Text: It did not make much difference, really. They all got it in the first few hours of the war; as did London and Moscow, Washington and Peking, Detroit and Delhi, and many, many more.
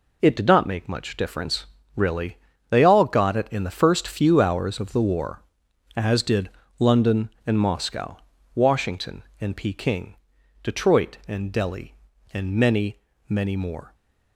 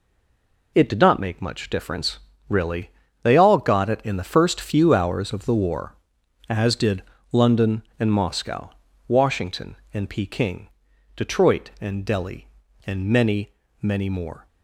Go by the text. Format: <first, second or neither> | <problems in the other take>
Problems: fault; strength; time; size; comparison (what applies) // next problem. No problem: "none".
first | stays silent before the first word; slight; until 0.7 s; 0.7 s long // pauses between "did" and "London"; slight; at 7.0 s; 0.30 s long; slight in the first